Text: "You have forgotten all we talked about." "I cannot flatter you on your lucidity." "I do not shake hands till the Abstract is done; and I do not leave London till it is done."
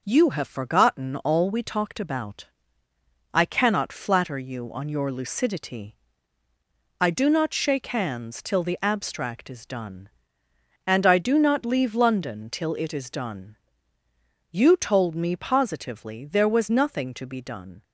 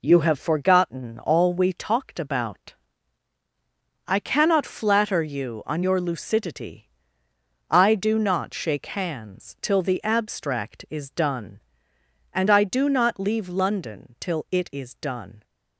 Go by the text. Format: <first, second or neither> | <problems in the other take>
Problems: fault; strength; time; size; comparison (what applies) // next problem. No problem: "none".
second | goes on to say "You told me positively there was nothing to be done"; strong; from 14.5 s on; 3.3 s long